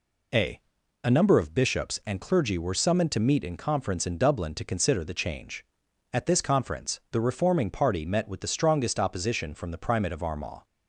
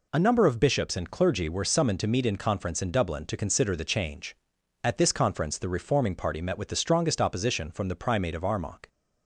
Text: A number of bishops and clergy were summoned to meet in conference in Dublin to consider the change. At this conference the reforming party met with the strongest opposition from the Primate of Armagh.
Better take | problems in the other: second | says "A" twice; at 1.0 s

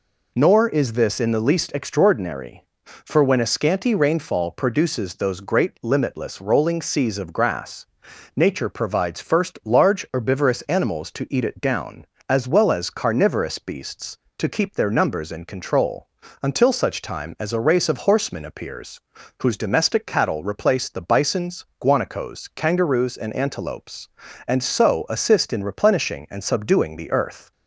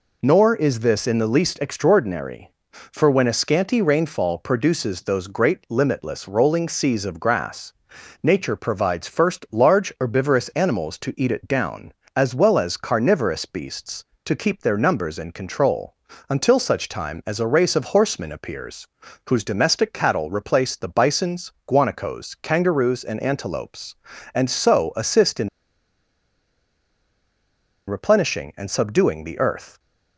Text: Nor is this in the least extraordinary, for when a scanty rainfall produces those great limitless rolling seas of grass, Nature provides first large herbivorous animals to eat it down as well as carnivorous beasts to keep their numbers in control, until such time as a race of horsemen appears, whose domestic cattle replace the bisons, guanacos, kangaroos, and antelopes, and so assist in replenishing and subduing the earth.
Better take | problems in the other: first | pauses between "in" and "replenishing"; strong; at 25.4 s; 2.3 s long

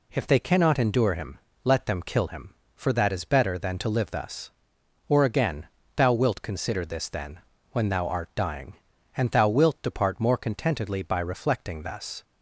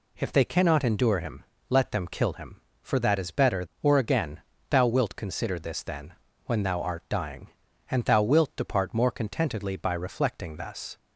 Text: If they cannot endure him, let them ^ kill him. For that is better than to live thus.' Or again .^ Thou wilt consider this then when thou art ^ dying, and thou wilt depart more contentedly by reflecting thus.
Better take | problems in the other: first | skips "than to live thus"; at 3.7 s // pauses between "then" and "when"; slight; at 6.1 s; 0.32 s long; slight in the first

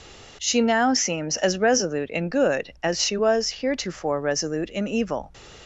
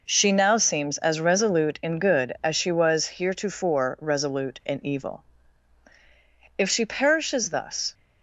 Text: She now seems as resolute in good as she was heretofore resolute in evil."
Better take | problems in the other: first | goes on to say "If she perishes thus"; from 6.5 s on; 1.3 s long

